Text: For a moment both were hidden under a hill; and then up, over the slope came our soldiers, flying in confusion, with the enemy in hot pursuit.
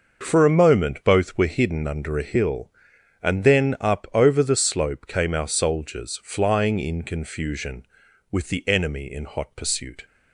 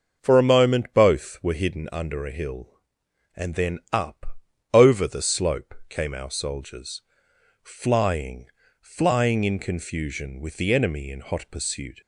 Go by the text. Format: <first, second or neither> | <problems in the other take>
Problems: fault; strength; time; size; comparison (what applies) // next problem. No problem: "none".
first | starts louder than the rest; until 1.2 s; 6.5 dB // pauses between "slope" and "came"; slight; at 5.7 s; 0.16 s long // says "flying" twice; at 8.8 s